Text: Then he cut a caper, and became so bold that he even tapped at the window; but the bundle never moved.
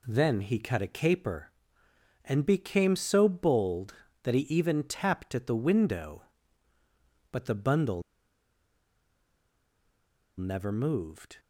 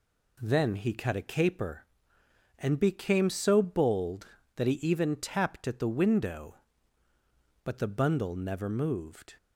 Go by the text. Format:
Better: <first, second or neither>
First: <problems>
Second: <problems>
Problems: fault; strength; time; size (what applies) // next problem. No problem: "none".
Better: second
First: pauses between "bundle" and "never"; strong; at 8.0 s; 2.3 s long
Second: none